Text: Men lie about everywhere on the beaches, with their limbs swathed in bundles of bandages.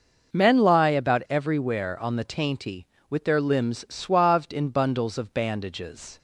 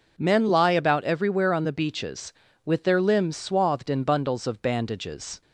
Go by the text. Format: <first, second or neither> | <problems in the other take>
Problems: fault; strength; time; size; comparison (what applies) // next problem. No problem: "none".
second | says "tainty" for "beaches"; at 2.2 s